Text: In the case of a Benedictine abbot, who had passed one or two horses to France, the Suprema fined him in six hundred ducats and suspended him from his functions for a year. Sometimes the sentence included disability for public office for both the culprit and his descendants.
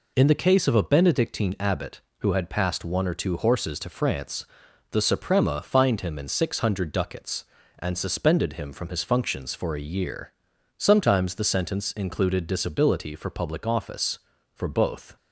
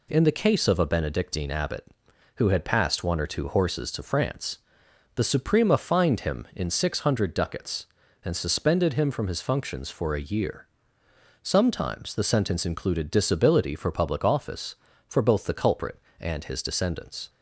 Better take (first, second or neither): second